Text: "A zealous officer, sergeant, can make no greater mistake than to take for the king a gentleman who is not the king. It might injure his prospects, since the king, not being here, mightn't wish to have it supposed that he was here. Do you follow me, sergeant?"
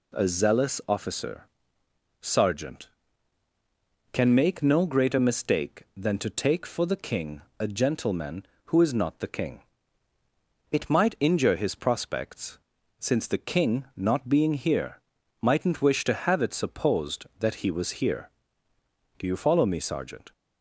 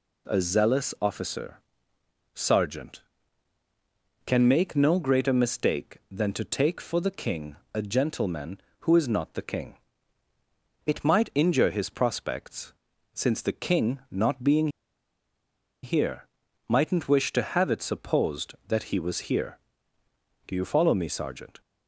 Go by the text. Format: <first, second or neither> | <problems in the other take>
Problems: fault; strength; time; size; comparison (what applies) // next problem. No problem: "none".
first | pauses between "king" and "a"; slight; at 7.5 s; 0.18 s long; slight in the first // pauses between "being" and "here"; at 14.6 s; 1.1 s long